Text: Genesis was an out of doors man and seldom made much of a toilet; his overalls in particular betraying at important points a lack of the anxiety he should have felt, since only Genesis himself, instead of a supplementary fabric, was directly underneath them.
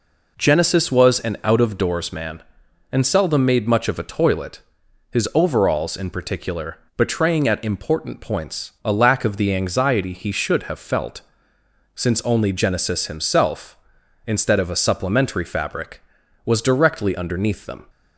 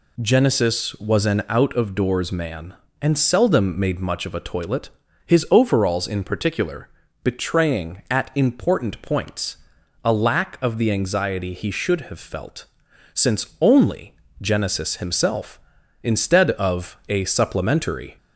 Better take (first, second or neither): first